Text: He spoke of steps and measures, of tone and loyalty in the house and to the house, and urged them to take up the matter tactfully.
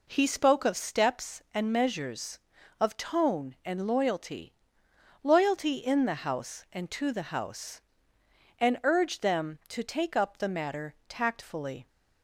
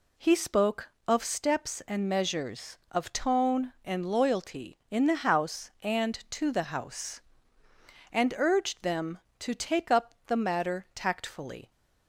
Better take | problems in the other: second | says "loyalty" twice; at 5.2 s

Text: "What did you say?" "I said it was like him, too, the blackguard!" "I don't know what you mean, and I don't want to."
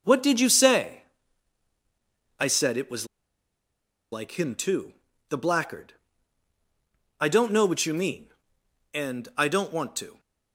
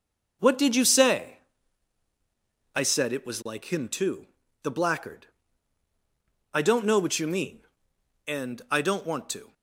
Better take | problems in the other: second | pauses between "was" and "like"; at 3.0 s; 1.0 s long

